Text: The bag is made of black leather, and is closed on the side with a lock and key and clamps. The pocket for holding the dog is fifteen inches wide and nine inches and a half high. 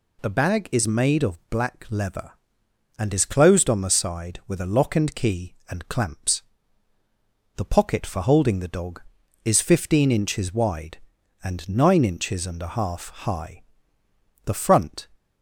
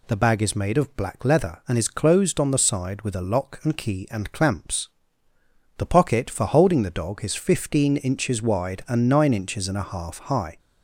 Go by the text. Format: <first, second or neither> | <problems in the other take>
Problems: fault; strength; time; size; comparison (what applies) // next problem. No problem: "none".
second | goes on to say "The front"; noticeable; from 14.4 s on; 0.64 s long